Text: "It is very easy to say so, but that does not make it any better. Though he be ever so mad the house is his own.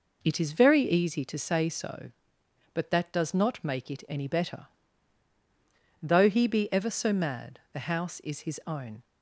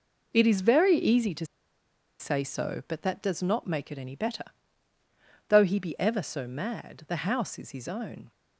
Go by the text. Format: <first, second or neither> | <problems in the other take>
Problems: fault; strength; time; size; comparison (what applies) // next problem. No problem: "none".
first | pauses between "to" and "say"; noticeable; at 1.4 s; 0.74 s long